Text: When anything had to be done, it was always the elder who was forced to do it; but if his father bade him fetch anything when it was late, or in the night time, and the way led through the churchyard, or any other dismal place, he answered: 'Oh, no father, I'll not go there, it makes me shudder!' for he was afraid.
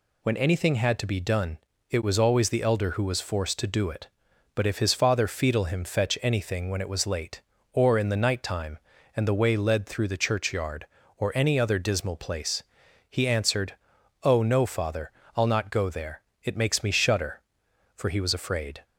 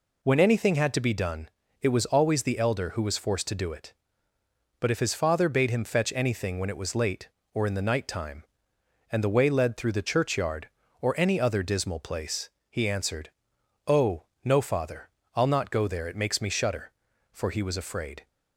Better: second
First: says "fetal" for "bade"; at 5.2 s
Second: none

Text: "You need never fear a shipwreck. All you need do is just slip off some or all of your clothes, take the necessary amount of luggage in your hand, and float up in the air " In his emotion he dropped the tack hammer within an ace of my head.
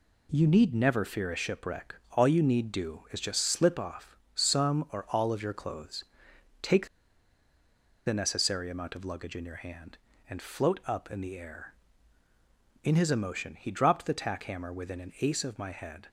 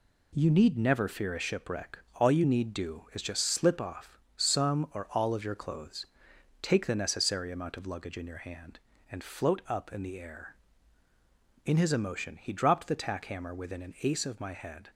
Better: second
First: pauses between "off" and "some"; slight; at 4.1 s; 0.16 s long // pauses between "take" and "the"; at 6.8 s; 1.1 s long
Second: pauses between "off" and "some"; slight; at 4.1 s; 0.16 s long

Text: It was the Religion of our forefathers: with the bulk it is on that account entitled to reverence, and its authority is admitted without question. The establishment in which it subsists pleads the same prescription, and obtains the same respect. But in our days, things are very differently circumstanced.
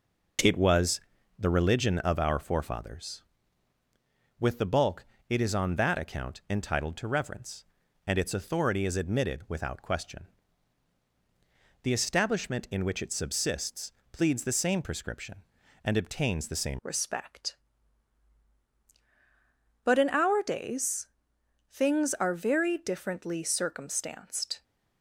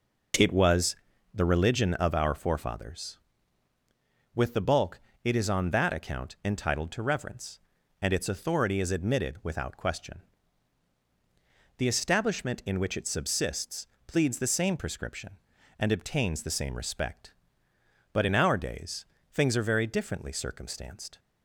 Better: second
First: pauses between "was" and "the"; slight; at 1.0 s; 0.36 s long // pauses between "bulk" and "it"; slight; at 5.0 s; 0.24 s long // pauses between "subsists" and "pleads"; slight; at 13.9 s; 0.20 s long // changes voice at "respect"; from 16.8 s on; 7.8 s long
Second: pauses between "was" and "the"; slight; at 0.9 s; 0.36 s long // pauses between "bulk" and "it"; slight; at 4.9 s; 0.24 s long // pauses between "subsists" and "pleads"; slight; at 13.8 s; 0.20 s long

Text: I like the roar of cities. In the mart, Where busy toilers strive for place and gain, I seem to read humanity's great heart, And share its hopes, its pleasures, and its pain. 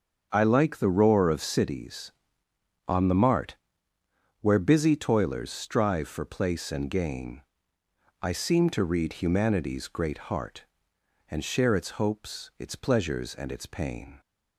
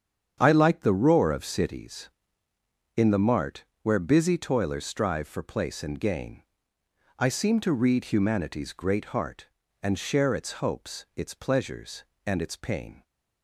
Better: second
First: starts louder than the rest; strong; until 1.3 s; 7 dB // says "On" for "In"; at 2.8 s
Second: starts louder than the rest; strong; until 1.4 s; 8 dB

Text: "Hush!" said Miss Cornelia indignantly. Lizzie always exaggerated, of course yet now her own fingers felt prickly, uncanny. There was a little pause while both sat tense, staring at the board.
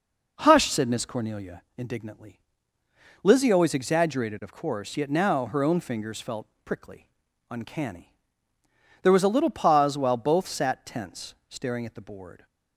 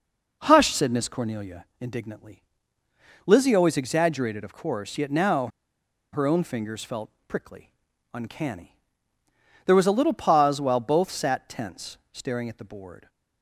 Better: first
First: pauses between "Cornelia" and "indignantly"; slight; at 1.6 s; 0.16 s long // pauses between "felt" and "prickly"; slight; at 6.4 s; 0.16 s long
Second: pauses between "Cornelia" and "indignantly"; slight; at 1.6 s; 0.16 s long // pauses between "now" and "her"; noticeable; at 5.4 s; 0.64 s long // pauses between "felt" and "prickly"; slight; at 7.1 s; 0.16 s long

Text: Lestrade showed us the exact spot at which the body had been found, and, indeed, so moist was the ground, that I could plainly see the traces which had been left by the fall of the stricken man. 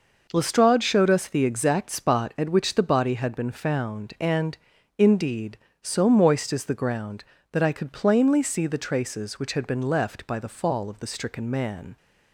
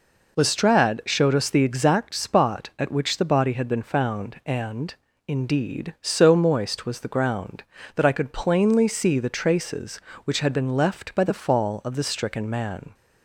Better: second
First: says "is" for "was"; at 6.5 s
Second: none

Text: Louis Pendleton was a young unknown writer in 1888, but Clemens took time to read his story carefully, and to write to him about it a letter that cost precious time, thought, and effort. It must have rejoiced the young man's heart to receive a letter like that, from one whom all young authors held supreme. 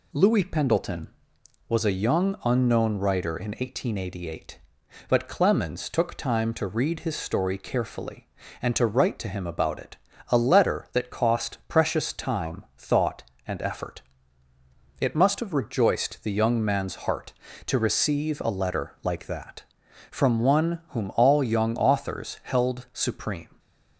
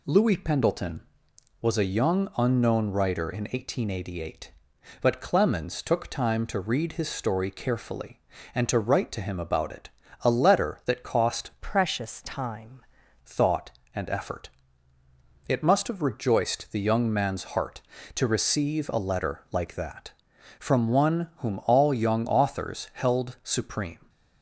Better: first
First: pauses between "it" and "a"; slight; at 9.9 s; 0.32 s long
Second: pauses between "it" and "a"; slight; at 9.8 s; 0.32 s long // changes voice from "precious" to "time"; from 11.6 to 12.7 s; 1.1 s long

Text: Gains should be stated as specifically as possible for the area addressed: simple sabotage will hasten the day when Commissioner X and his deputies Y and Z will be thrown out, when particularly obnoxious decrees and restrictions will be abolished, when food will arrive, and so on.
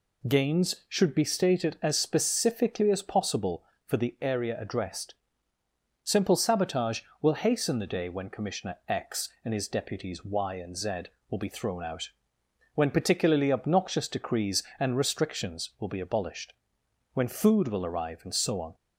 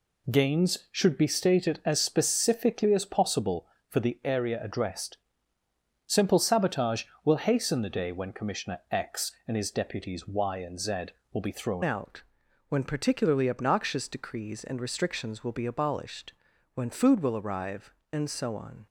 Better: first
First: none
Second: changes voice at "out"; from 11.8 s on; 7.0 s long

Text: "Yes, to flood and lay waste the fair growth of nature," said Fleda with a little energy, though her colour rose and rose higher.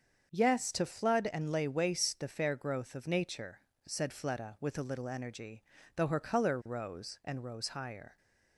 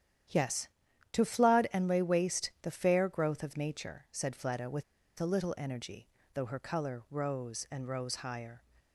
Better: first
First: starts louder than the rest; until 1.3 s; 7 dB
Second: starts louder than the rest; strong; until 1.7 s; 10 dB // pauses between "with" and "a"; at 4.8 s; 0.36 s long

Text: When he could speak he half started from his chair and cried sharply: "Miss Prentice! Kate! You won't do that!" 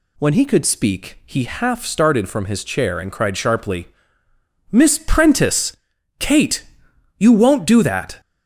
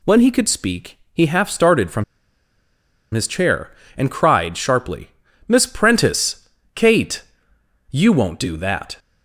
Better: first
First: none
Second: pauses between "speak" and "he"; slight; at 0.9 s; 0.16 s long // pauses between "from" and "his"; at 2.0 s; 1.1 s long

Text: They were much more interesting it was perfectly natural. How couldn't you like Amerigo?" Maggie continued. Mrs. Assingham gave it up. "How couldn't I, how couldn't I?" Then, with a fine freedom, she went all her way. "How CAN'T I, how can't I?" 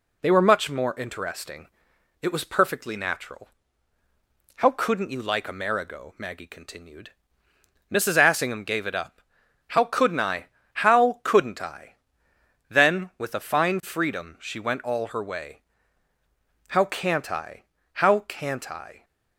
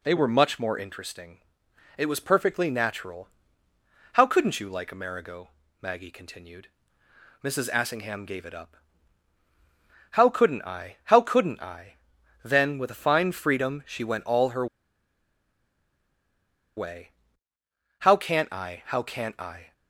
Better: first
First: pauses between "interesting" and "it"; noticeable; at 1.6 s; 0.52 s long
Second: pauses between "interesting" and "it"; noticeable; at 1.3 s; 0.58 s long // pauses between "her" and "way"; strong; at 14.6 s; 2.1 s long

